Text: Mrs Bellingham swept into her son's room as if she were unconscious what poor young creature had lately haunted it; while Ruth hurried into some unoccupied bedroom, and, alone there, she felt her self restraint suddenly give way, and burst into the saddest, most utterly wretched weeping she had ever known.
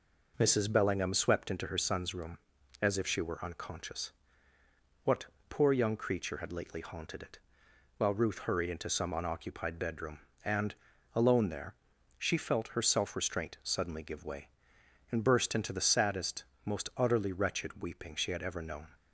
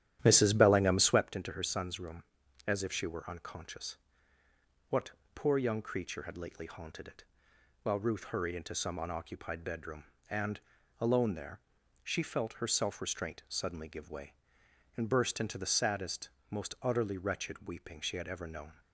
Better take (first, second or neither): first